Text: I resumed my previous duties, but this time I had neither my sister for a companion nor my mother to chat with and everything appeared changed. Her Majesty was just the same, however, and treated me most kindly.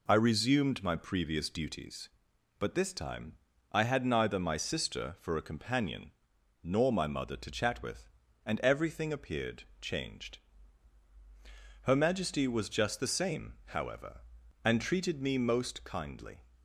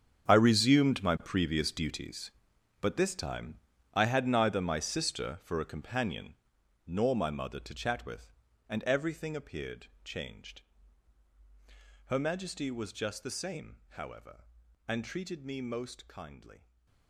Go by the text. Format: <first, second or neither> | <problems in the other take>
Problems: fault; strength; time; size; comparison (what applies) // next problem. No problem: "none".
first | gets quieter; strong; throughout; 14.5 dB // pauses between "time" and "I"; at 3.5 s; 0.40 s long; also in the first // pauses between "companion" and "nor"; noticeable; at 6.3 s; 0.52 s long; noticeable in the first // pauses between "appeared" and "changed"; slight; at 9.8 s; 0.18 s long; slight in the first // stays silent after the last word; slight; from 16.5 s on; 0.5 s long